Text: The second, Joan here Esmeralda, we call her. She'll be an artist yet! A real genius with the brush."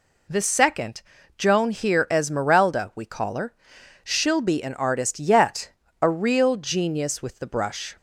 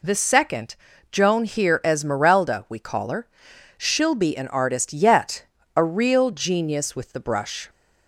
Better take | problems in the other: neither | none

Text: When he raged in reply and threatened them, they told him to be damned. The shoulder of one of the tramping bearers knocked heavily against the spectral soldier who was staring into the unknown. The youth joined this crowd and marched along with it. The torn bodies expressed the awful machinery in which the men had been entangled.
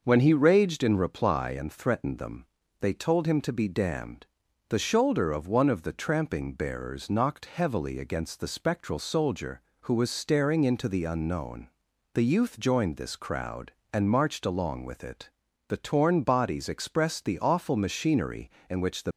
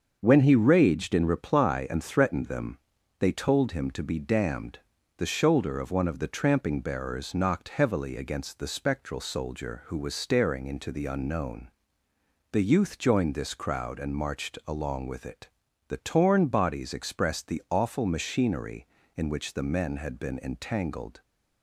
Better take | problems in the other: second | starts louder than the rest; noticeable; until 1.0 s; 6 dB; also in the second // stops before "men had been entangled"; at 19.1 s

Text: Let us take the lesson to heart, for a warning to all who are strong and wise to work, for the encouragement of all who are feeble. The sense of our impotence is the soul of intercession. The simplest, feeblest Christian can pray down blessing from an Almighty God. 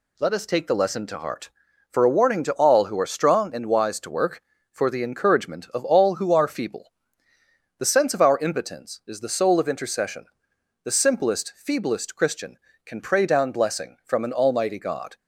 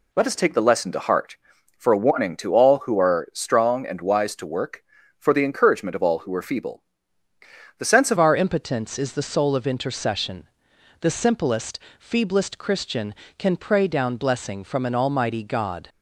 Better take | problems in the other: first | changes voice at "our"; from 8.1 s on; 7.7 s long

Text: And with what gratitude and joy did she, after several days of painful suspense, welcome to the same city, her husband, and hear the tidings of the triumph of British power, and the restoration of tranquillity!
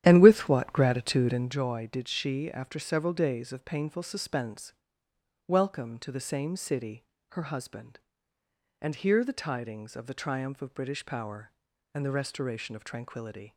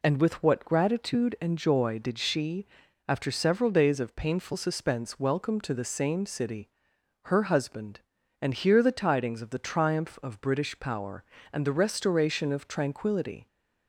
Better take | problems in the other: second | starts louder than the rest; strong; until 1.6 s; 11 dB

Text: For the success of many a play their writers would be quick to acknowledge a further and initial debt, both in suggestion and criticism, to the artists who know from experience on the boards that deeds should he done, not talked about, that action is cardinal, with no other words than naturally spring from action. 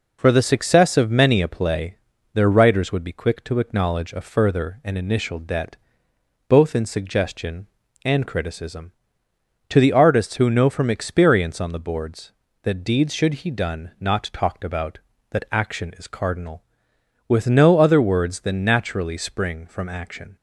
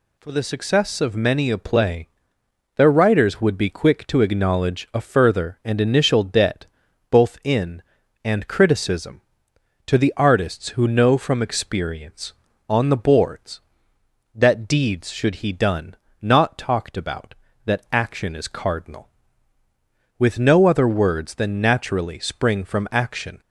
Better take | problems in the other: first | pauses between "play" and "their"; noticeable; at 2.0 s; 0.66 s long; also in the first // skips "suggestion"; at 8.0 s

